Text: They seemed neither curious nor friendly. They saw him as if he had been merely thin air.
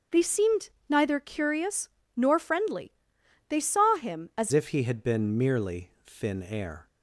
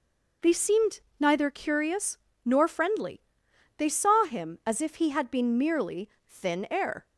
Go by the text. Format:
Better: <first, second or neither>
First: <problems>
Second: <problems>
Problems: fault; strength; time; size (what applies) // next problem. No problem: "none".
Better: second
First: starts louder than the rest; until 1.3 s; 6 dB // pauses between "seemed" and "neither"; slight; at 0.6 s; 0.18 s long // pauses between "curious" and "nor"; slight; at 1.8 s; 0.26 s long // changes voice at "if"; from 4.5 s on; 2.3 s long // pauses between "merely" and "thin"; slight; at 5.9 s; 0.16 s long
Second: pauses between "seemed" and "neither"; slight; at 0.9 s; 0.18 s long // pauses between "curious" and "nor"; slight; at 2.1 s; 0.26 s long // pauses between "merely" and "thin"; slight; at 6.1 s; 0.18 s long